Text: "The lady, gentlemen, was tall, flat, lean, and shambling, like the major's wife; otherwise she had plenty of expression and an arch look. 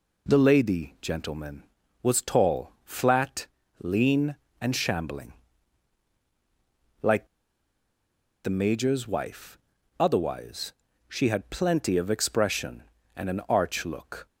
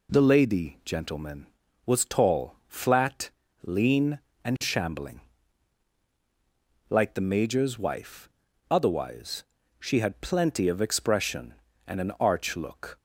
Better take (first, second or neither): second